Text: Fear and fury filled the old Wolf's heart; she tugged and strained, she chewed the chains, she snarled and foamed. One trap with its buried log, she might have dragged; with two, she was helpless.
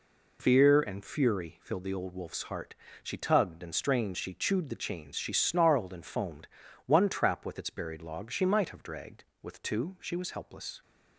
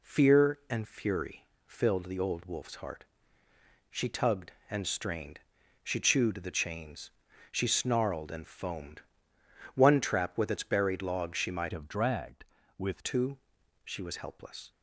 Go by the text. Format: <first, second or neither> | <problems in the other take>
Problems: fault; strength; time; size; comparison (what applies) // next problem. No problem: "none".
first | pauses between "fury" and "filled"; slight; at 1.4 s; 0.22 s long // changes voice from "have" to "with"; from 11.7 to 13.0 s; 1.3 s long